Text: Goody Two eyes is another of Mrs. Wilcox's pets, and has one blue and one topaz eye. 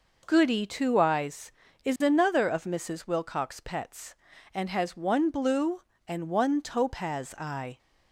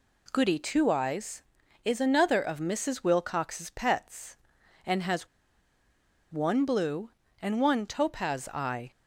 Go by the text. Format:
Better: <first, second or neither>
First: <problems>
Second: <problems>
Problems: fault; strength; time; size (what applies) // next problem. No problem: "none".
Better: first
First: none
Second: pauses between "has" and "one"; at 5.2 s; 1.0 s long